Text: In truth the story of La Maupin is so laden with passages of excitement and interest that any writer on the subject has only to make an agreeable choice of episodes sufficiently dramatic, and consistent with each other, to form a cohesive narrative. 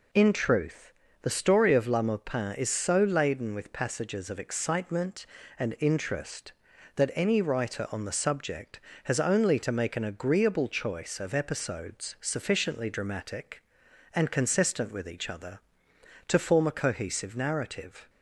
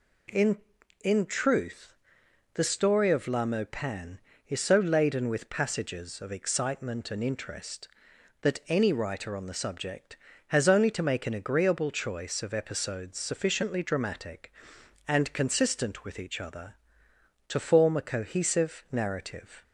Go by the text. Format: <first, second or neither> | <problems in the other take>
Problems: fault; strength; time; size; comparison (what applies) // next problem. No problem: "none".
first | says "In" twice; at 1.0 s // pauses between "truth" and "the"; noticeable; at 1.9 s; 0.58 s long; slight in the first